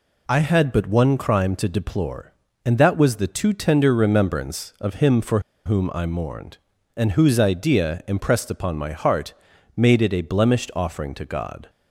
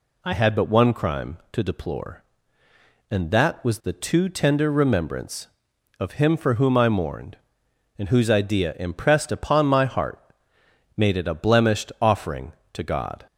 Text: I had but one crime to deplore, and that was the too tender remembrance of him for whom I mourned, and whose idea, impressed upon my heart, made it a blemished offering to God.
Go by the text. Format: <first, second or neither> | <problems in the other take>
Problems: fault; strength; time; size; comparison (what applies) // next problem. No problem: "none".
second | pauses between "for" and "whom"; slight; at 5.4 s; 0.25 s long